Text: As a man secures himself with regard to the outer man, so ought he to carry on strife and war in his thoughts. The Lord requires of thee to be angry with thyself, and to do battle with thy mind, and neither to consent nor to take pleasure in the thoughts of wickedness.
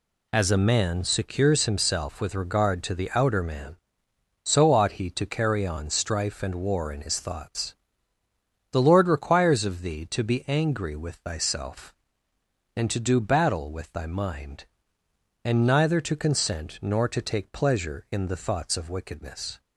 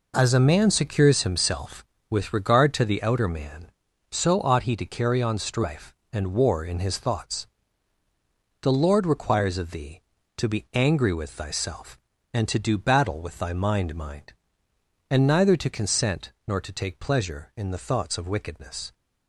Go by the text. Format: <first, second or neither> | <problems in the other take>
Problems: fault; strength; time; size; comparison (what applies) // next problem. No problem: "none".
first | says "mind" twice; at 13.9 s // pauses between "consent" and "nor"; slight; at 16.3 s; 0.16 s long